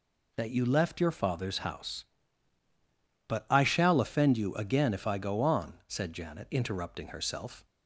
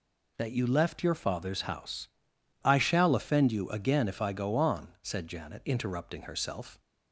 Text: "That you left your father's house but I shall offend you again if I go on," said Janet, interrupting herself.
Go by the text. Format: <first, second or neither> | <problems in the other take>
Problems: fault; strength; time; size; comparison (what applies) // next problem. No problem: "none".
first | skips "but"; at 2.3 s